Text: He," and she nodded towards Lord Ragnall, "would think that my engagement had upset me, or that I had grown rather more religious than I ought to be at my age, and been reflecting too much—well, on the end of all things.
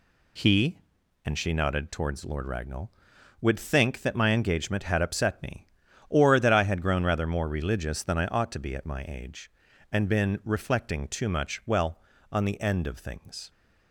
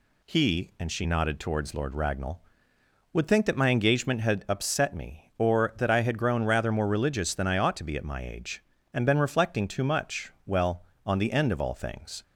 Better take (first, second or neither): second